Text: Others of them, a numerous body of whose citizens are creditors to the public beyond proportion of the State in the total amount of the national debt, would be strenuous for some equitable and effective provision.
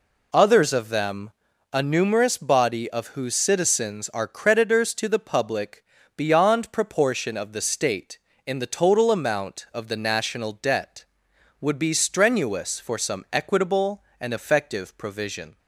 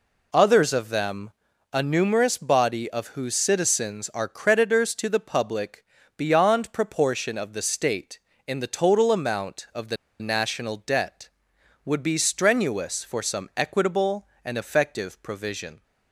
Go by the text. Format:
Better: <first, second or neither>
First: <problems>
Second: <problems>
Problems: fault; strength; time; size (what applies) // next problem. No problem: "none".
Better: first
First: pauses between "public" and "beyond"; slight; at 5.8 s; 0.34 s long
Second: pauses between "public" and "beyond"; slight; at 5.8 s; 0.34 s long // pauses between "the" and "national"; slight; at 9.9 s; 0.24 s long